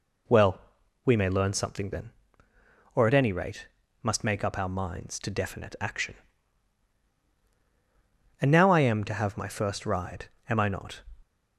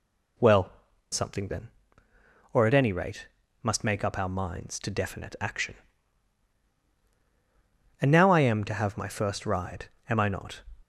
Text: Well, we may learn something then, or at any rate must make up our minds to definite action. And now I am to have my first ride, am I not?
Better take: first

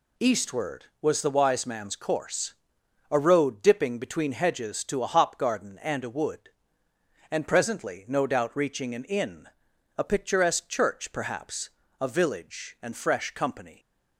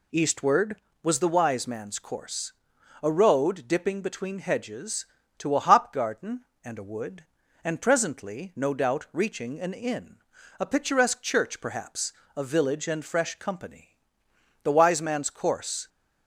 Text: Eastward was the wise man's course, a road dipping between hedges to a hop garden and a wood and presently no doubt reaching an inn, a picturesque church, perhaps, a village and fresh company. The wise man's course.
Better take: second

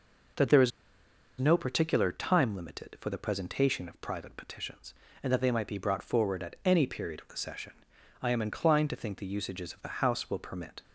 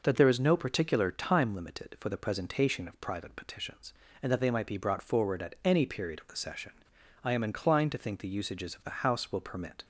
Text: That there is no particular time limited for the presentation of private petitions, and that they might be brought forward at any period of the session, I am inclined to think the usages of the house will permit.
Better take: second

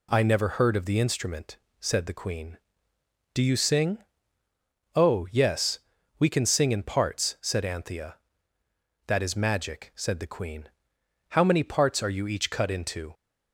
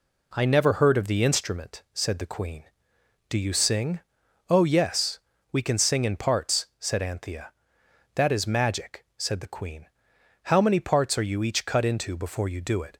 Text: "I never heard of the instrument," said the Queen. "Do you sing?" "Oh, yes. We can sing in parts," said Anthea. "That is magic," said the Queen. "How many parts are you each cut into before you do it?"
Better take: second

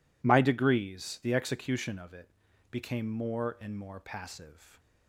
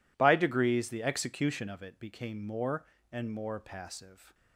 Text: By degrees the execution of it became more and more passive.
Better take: second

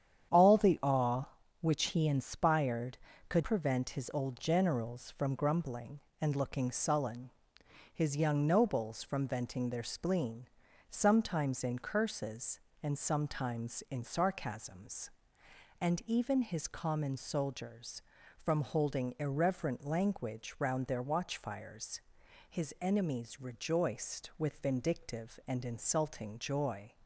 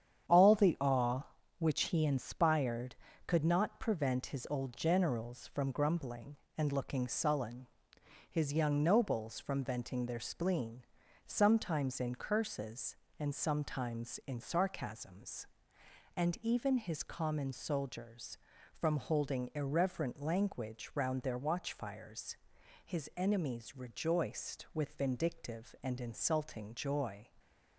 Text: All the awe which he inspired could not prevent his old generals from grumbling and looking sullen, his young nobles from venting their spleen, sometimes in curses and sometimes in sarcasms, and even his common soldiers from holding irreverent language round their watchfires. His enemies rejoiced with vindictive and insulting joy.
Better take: second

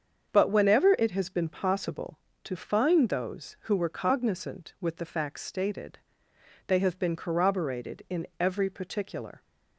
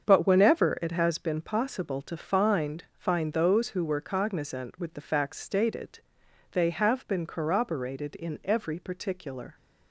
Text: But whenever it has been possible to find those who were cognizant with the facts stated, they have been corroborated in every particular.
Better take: first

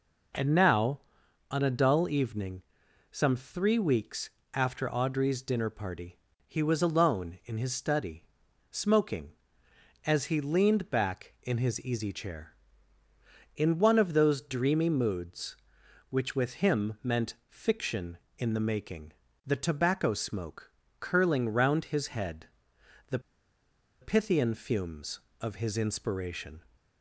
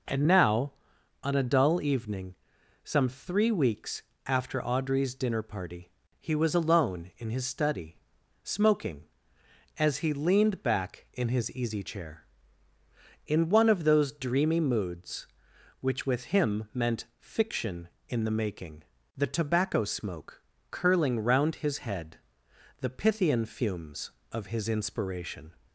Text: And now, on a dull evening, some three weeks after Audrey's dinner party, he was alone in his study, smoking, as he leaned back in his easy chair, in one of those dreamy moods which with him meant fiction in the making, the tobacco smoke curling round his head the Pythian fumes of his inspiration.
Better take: second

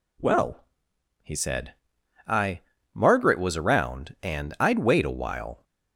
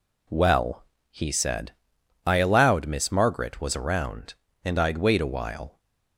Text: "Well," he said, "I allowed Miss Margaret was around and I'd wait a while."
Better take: second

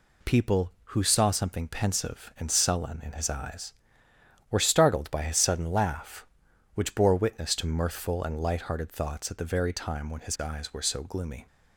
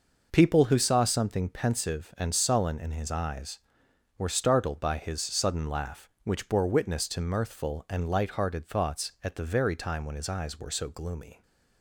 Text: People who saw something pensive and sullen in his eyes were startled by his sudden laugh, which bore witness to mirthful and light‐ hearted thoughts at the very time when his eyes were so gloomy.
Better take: neither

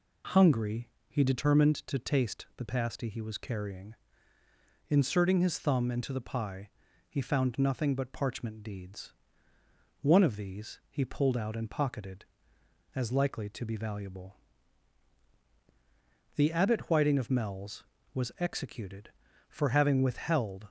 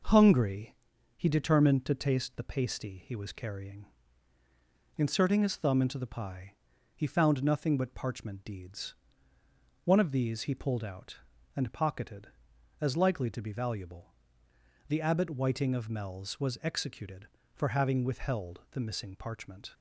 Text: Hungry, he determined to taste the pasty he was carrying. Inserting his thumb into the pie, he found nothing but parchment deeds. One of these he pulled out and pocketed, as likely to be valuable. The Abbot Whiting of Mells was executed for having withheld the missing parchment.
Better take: second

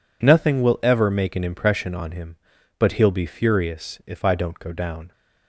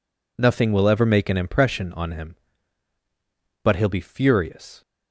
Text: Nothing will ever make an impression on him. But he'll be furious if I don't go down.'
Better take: first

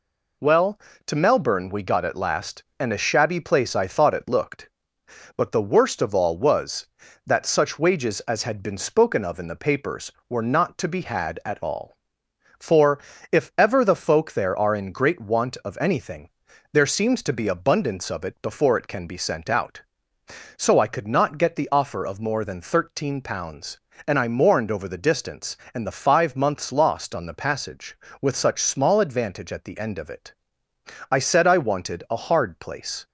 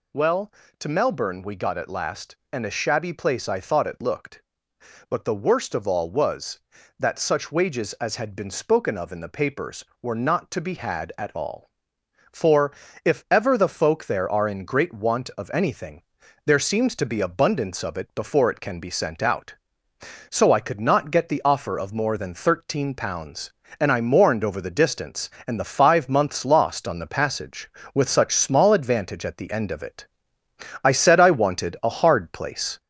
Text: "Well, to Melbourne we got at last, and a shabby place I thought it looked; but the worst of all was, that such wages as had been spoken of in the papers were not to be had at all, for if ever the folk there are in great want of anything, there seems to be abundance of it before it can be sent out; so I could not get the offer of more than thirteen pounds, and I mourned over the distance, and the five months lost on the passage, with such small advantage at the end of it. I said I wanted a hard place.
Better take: first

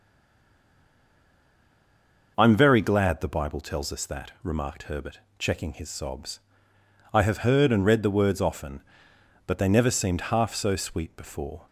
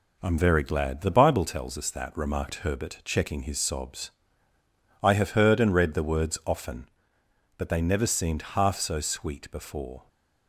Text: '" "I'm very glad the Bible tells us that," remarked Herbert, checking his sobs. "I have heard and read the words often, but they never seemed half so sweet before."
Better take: second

